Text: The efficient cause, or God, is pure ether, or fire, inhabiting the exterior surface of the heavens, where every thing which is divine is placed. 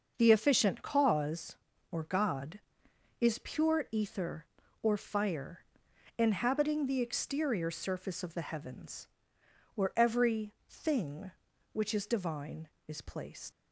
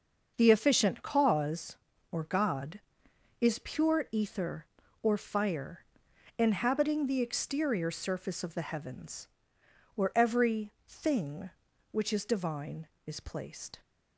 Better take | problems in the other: second | starts louder than the rest; until 1.1 s; 6 dB; also in the second // pauses between "every" and "thing"; slight; at 10.5 s; 0.16 s long; slight in the second // leaves "placed" unfinished; at 13.5 s; 115 ms

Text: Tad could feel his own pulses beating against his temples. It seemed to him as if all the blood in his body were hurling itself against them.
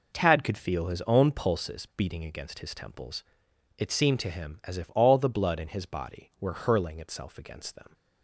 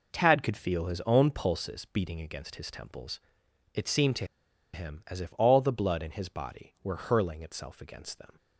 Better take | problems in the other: first | pauses between "to" and "him"; noticeable; at 4.2 s; 0.47 s long

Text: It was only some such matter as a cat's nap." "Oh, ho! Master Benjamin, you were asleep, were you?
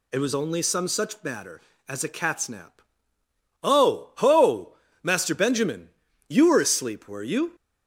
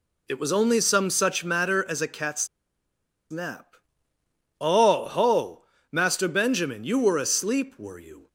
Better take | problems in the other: first | pauses between "cat's" and "nap"; noticeable; at 2.4 s; 0.84 s long

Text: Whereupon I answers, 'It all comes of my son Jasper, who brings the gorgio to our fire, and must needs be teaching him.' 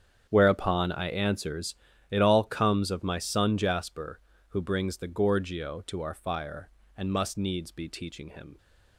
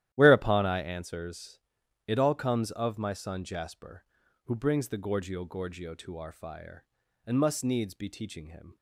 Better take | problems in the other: first | starts louder than the rest; strong; until 1.1 s; 12.5 dB; strong in the first // says "gorgio" twice; at 5.4 s

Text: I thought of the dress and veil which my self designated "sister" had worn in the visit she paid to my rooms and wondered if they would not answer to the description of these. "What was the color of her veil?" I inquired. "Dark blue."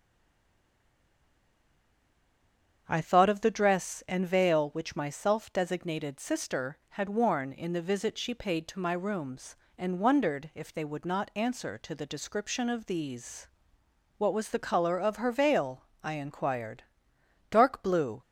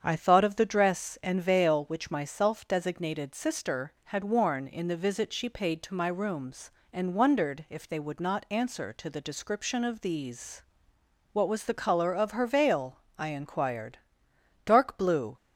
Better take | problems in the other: second | stays silent before the first word; strong; until 2.8 s; 2.8 s long // starts louder than the rest; strong; until 3.8 s; 7.5 dB; strong in the second

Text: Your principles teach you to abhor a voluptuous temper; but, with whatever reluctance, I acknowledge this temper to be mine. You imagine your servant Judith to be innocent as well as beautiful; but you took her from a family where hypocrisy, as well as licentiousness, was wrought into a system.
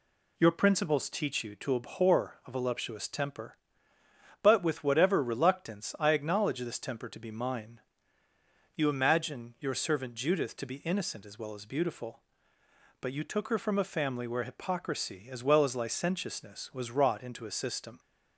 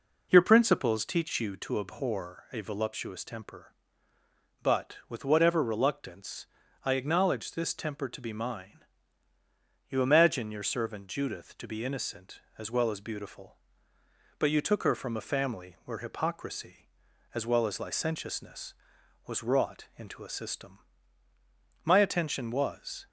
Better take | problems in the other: first | goes on to say "My attention was"; noticeable; from 21.8 s on; 1.2 s long

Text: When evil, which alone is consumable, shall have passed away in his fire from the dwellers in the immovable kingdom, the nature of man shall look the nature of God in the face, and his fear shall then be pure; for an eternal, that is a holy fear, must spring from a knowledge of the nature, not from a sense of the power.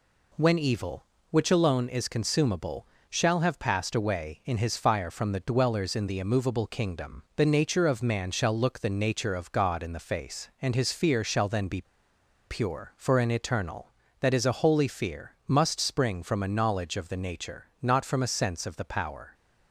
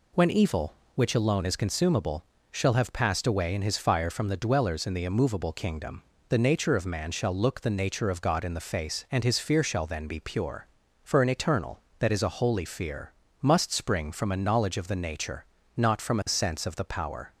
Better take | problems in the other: second | pauses between "be" and "pure"; noticeable; at 11.8 s; 0.65 s long

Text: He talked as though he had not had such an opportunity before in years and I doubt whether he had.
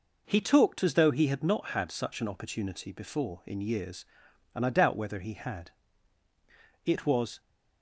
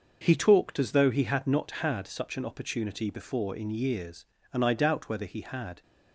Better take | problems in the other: second | goes on to say "It was"; from 6.8 s on; 0.56 s long

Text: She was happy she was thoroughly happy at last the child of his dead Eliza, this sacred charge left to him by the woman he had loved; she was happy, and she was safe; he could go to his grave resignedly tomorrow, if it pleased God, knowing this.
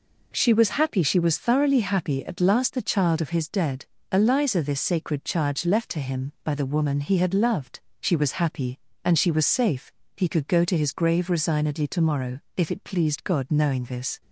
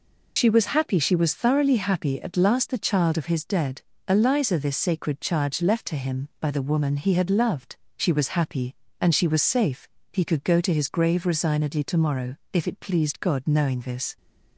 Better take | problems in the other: first | loses the start of "She"; at 0.3 s; 65 ms // pauses between "dead" and "Eliza"; slight; at 3.8 s; 0.26 s long; slight in the first

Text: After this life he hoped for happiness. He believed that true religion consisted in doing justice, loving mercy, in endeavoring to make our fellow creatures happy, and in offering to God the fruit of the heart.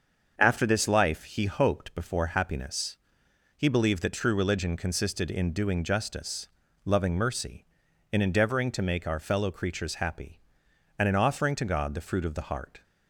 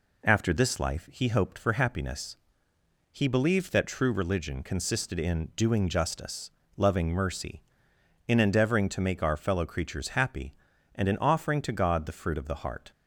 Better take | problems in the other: second | starts louder than the rest; until 1.3 s; 6.5 dB // says "before" for "for"; at 1.9 s

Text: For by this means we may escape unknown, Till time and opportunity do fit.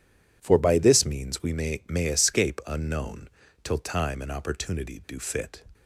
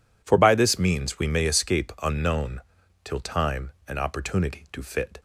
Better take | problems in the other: second | says "may" twice; at 1.8 s

